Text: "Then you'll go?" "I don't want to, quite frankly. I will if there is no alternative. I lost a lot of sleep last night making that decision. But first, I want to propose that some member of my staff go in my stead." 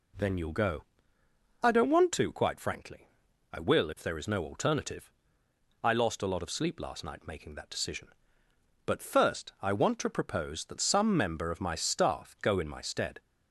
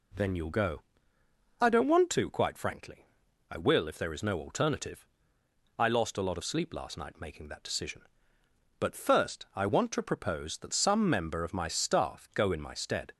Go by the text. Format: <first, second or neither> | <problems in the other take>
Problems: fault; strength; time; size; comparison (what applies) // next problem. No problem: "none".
neither | none